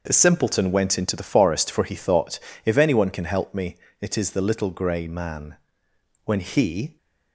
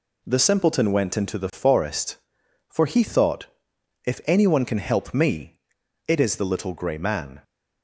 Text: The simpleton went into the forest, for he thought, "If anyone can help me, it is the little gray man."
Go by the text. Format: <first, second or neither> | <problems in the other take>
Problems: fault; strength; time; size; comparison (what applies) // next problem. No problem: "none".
second | goes on to say "When he"; noticeable; from 6.2 s on; 0.72 s long